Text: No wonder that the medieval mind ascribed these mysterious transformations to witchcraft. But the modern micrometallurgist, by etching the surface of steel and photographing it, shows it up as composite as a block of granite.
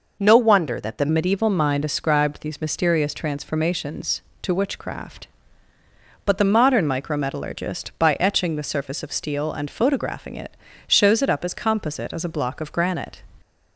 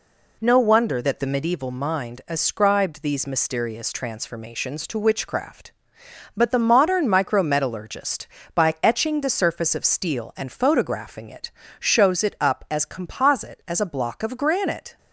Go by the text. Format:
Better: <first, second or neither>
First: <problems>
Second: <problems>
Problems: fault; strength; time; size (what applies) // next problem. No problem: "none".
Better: second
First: changes voice at "medieval"; from 1.1 s on; 12.1 s long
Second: none